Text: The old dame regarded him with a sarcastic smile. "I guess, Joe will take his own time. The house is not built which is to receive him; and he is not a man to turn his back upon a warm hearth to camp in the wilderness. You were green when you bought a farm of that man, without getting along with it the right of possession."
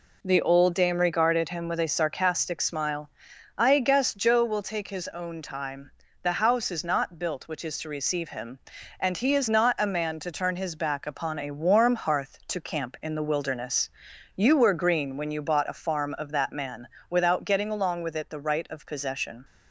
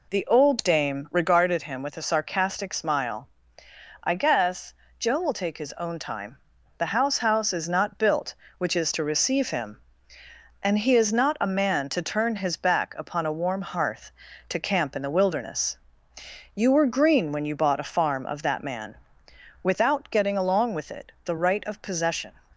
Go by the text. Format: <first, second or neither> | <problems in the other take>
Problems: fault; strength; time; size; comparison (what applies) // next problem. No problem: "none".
first | says "house" twice; at 7.1 s